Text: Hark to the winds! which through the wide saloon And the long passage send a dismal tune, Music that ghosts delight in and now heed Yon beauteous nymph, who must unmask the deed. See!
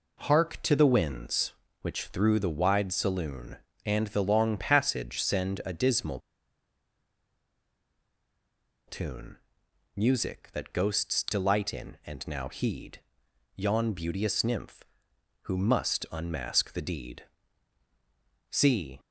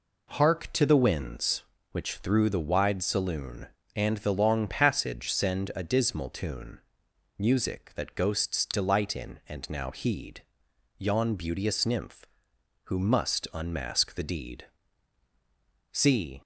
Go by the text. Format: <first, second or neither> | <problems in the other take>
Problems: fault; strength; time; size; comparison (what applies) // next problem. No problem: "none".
second | pauses between "dismal" and "tune"; strong; at 6.1 s; 2.6 s long // pauses between "heed" and "Yon"; noticeable; at 12.9 s; 0.56 s long; noticeable in the second